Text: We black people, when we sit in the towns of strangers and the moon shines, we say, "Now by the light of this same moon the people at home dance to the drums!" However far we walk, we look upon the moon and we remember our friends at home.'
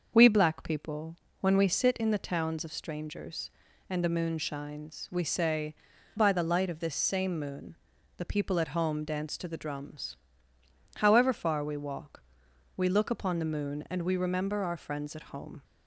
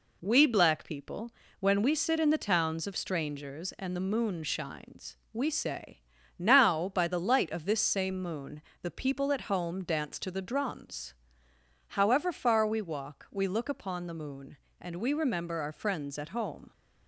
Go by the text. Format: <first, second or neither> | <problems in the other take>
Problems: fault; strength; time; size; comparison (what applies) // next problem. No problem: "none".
second | starts louder than the rest; until 1.1 s; 6.5 dB // skips "Now"; at 5.9 s // pauses between "moon" and "the"; at 7.7 s; 0.44 s long; slight in the second